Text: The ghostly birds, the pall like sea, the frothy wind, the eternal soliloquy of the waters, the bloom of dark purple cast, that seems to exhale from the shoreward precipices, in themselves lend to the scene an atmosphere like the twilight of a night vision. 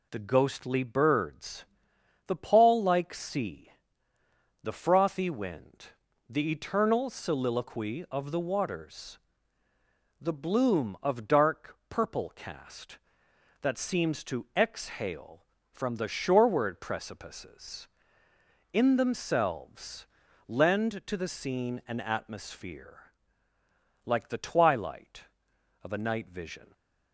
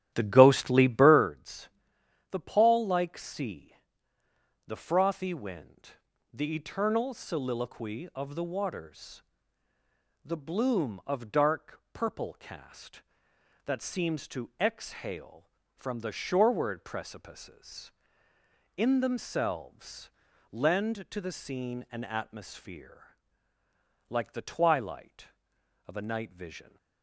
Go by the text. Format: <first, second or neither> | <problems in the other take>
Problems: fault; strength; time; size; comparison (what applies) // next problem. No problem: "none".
first | starts louder than the rest; strong; until 1.3 s; 12 dB // pauses between "themselves" and "lend"; at 20.1 s; 0.40 s long; also in the first // pauses between "atmosphere" and "like"; noticeable; at 23.1 s; 0.96 s long; noticeable in the first